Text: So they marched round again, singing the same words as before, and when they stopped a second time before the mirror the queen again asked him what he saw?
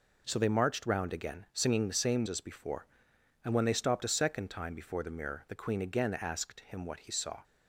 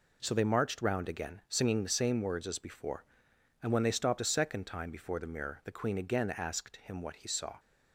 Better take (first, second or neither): second